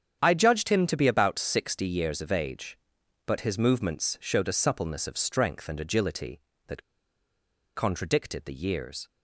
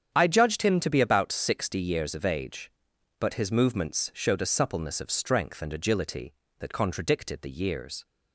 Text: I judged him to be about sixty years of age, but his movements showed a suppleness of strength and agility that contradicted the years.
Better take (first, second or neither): second